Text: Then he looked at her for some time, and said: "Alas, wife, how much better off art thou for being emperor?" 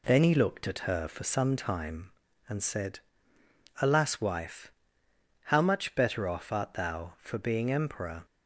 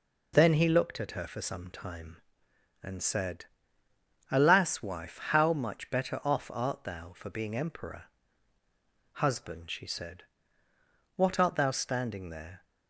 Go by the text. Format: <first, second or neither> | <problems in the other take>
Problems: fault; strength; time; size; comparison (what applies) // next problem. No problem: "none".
first | goes on to say "Husband she said what art thou standing there"; strong; from 9.1 s on; 3.5 s long